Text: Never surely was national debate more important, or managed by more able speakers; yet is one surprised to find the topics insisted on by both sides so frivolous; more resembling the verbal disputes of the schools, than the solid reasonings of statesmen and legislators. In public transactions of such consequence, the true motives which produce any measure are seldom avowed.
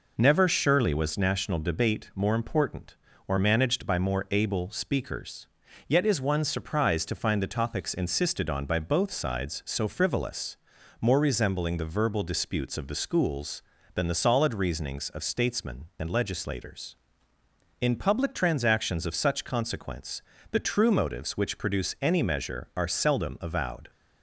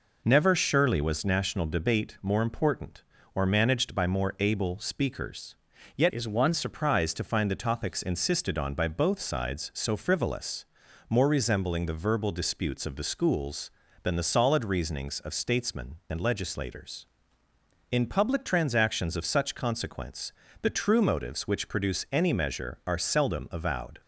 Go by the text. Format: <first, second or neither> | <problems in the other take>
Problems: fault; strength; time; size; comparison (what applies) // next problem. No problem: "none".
first | changes voice from "is" to "one"; from 6.1 to 6.5 s; 0.4 s long